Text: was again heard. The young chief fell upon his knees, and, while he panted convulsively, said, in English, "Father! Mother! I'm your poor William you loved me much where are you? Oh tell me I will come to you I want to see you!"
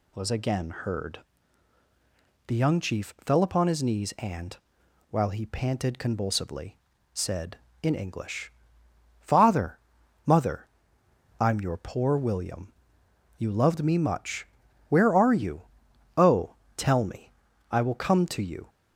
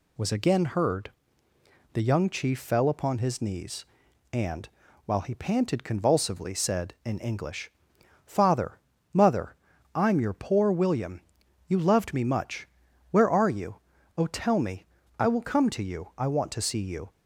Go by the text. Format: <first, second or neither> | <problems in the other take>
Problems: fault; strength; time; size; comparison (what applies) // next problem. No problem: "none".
second | pauses between "William" and "you"; noticeable; at 12.7 s; 0.68 s long; noticeable in the second // pauses between "much" and "where"; at 14.4 s; 0.44 s long; also in the second // pauses between "Oh" and "tell"; slight; at 16.5 s; 0.20 s long // pauses between "me" and "I"; at 17.3 s; 0.40 s long; slight in the second // stops before "I want to see you"; at 18.6 s